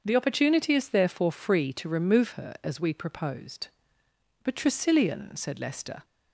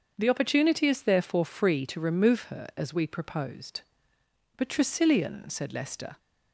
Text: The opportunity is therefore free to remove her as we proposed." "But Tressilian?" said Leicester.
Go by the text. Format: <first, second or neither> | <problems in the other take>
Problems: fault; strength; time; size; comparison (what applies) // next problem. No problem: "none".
neither | starts louder than the rest; the same in both